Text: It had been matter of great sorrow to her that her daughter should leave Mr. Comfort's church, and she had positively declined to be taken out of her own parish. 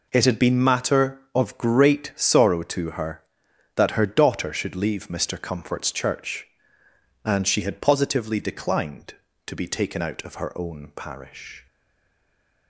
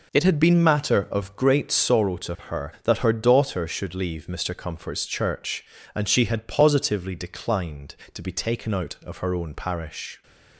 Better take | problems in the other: second | stays silent after the last word; from 11.6 s on; 1.0 s long

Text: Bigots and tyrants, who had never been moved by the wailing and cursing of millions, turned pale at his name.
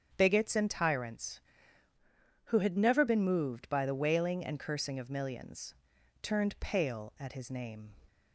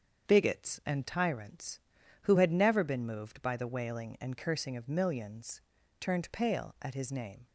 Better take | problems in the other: second | starts louder than the rest; strong; until 1.1 s; 8.5 dB; strong in the second // changes voice from "who" to "never"; from 2.4 to 3.0 s; 0.6 s long

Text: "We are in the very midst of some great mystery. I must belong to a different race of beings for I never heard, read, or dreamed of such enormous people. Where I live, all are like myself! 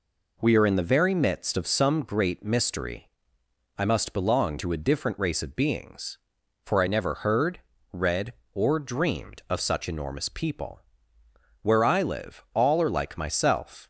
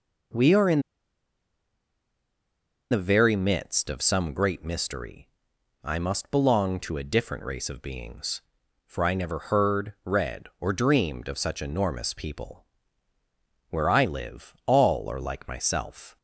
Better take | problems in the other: first | pauses between "in" and "the"; strong; at 0.7 s; 2.1 s long

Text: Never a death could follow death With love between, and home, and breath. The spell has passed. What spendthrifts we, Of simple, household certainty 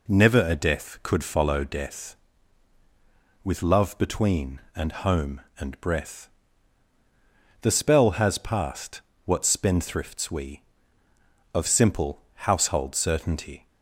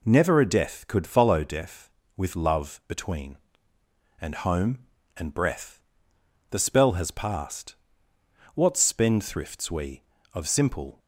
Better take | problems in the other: first | stops before "household certainty"; at 10.9 s

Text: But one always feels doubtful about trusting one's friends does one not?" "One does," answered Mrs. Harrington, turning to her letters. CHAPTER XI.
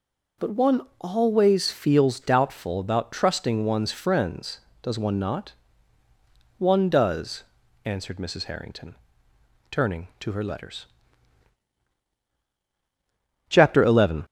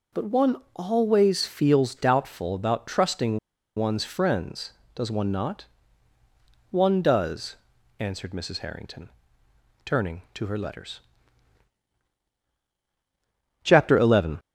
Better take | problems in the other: first | pauses between "one" and "always"; slight; at 0.5 s; 0.18 s long; slight in the first // pauses between "trusting" and "one's"; at 3.3 s; 0.38 s long

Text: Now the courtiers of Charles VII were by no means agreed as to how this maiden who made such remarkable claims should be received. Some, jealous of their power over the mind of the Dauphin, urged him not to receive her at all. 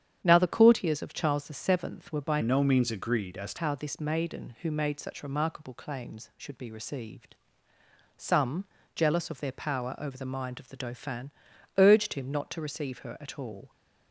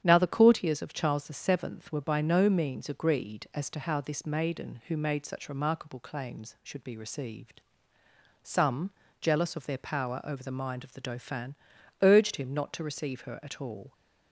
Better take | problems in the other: second | starts louder than the rest; strong; until 1.2 s; 9 dB; strong in the second // changes voice from "no" to "to"; from 2.4 to 3.5 s; 1.1 s long

